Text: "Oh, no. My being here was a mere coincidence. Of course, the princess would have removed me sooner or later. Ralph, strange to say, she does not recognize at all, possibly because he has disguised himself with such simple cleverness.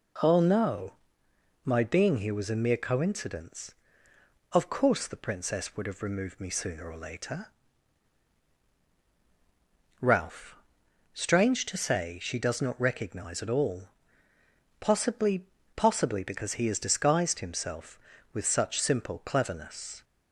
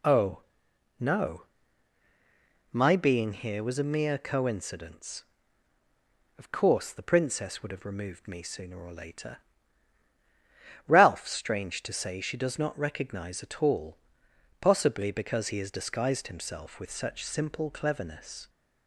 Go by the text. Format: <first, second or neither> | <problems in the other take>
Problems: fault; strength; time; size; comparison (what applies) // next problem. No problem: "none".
second | says "possibly" twice; at 15.7 s